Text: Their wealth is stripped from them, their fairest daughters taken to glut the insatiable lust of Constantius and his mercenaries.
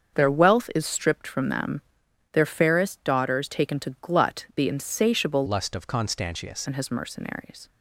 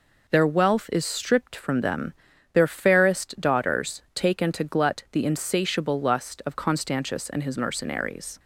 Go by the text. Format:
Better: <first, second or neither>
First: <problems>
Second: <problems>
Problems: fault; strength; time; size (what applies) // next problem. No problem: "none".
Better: second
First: starts louder than the rest; until 1.2 s; 7 dB // changes voice from "lust" to "Constantius"; from 5.4 to 6.6 s; 1.2 s long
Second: none